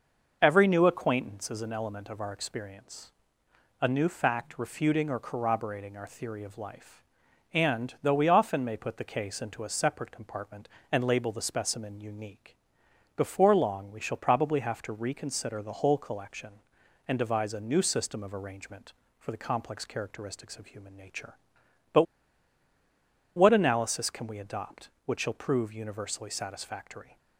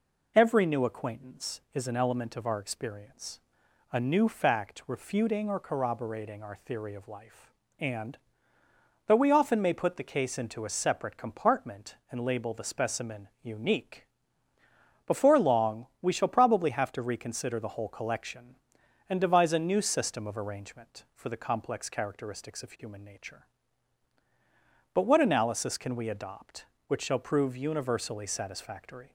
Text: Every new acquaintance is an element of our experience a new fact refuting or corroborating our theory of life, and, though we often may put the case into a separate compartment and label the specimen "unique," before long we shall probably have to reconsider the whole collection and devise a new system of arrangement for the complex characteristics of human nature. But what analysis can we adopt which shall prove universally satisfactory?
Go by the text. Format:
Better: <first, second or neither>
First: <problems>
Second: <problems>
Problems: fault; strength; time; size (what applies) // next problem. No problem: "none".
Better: second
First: pauses between "experience" and "a"; noticeable; at 3.1 s; 0.70 s long // pauses between "But" and "what"; strong; at 22.0 s; 1.3 s long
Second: pauses between "experience" and "a"; noticeable; at 3.3 s; 0.52 s long